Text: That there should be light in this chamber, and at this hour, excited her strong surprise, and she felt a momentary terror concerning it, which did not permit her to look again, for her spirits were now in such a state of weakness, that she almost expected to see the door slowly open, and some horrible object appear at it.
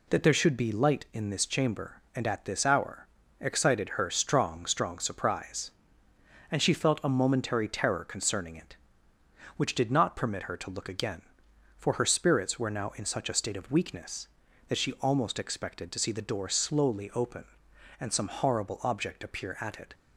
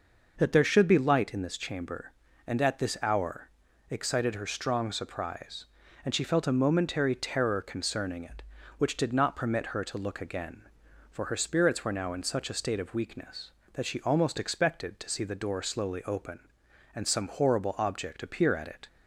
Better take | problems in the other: second | says "strong" twice; at 4.6 s

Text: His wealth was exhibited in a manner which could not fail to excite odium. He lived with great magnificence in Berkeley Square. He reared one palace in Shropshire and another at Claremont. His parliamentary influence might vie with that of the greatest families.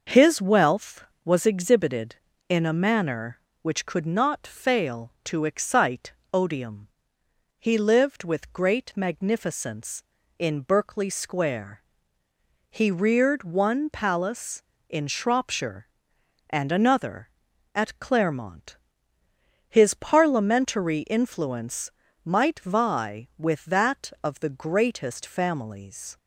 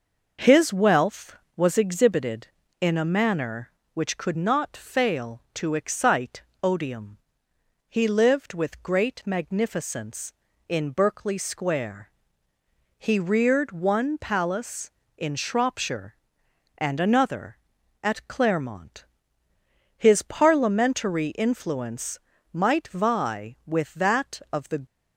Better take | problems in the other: first | pauses between "excite" and "odium"; slight; at 6.4 s; 0.18 s long; slight in the first // pauses between "influence" and "might"; slight; at 22.1 s; 0.34 s long; slight in the first // stops before "greatest families"; at 24.8 s

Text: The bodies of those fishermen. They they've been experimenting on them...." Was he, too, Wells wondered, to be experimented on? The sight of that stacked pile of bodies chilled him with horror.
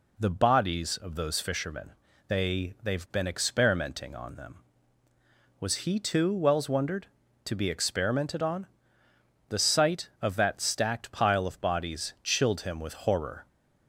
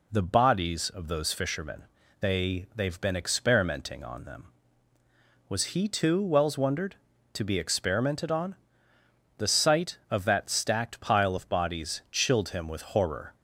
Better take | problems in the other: neither | none

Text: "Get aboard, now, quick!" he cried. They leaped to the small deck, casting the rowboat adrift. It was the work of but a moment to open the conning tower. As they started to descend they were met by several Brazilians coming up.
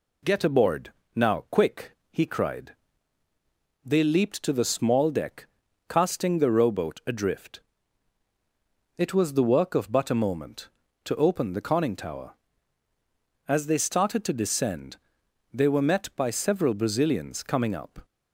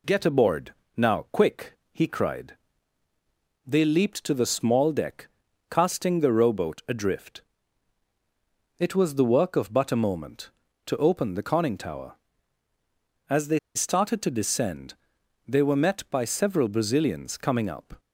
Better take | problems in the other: first | pauses between "they" and "started"; slight; at 13.5 s; 0.16 s long // pauses between "descend" and "they"; noticeable; at 14.9 s; 0.54 s long; noticeable in the first

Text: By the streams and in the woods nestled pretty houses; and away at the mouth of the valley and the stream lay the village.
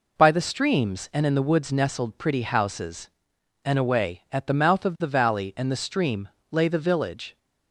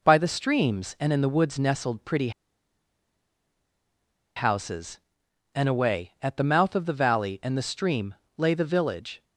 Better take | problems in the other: first | pauses between "pretty" and "houses"; strong; at 2.3 s; 2.0 s long // pauses between "stream" and "lay"; slight; at 8.1 s; 0.24 s long; slight in the first

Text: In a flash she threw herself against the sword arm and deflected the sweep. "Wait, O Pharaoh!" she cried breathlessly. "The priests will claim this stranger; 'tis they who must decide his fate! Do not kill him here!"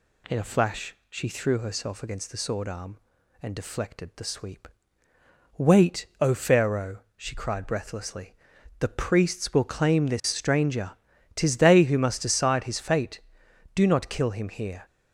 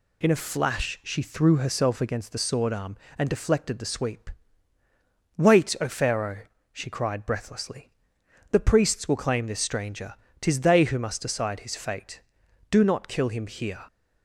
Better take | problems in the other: neither | none

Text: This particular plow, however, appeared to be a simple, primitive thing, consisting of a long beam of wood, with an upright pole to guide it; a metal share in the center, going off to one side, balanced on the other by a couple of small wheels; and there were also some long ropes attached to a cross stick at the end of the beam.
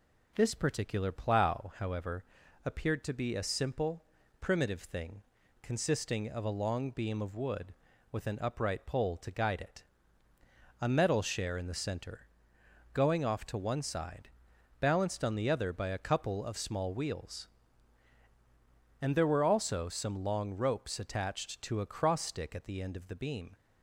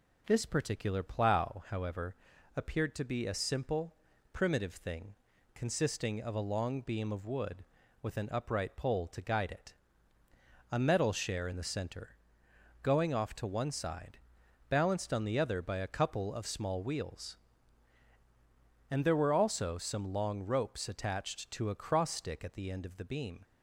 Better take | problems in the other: neither | none

